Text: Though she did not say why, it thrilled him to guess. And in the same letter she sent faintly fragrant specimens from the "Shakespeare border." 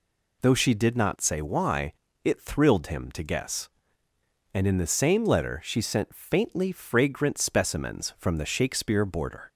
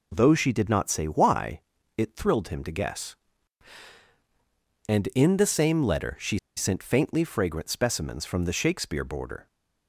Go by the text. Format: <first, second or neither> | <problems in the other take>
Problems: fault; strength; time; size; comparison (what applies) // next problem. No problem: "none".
first | pauses between "she" and "sent"; slight; at 6.3 s; 0.17 s long